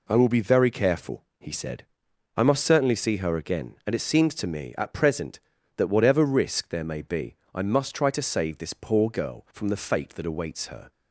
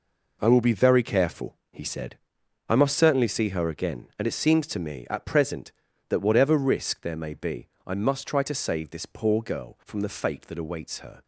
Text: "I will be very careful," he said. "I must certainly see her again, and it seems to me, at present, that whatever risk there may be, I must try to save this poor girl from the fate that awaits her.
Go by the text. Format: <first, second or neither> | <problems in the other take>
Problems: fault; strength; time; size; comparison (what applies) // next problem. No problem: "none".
first | gets quieter; strong; throughout; 10.5 dB